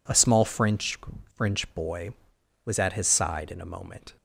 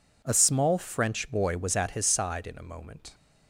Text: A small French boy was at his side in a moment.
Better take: second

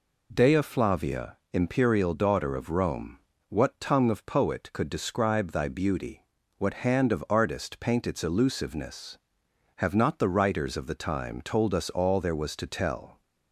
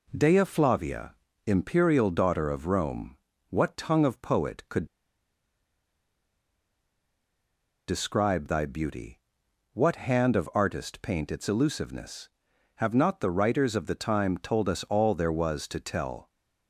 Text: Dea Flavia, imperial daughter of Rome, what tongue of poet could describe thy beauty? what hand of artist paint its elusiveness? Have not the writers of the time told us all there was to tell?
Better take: first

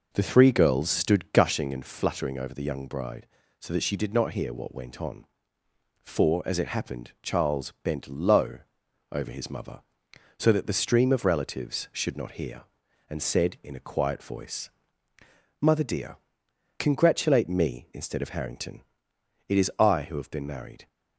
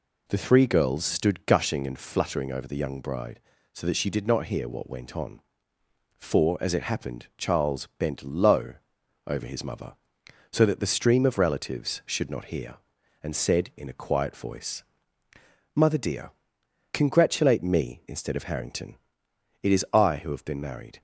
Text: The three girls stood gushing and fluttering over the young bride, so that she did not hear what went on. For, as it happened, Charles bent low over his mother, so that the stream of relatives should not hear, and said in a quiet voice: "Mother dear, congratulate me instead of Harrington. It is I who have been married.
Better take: second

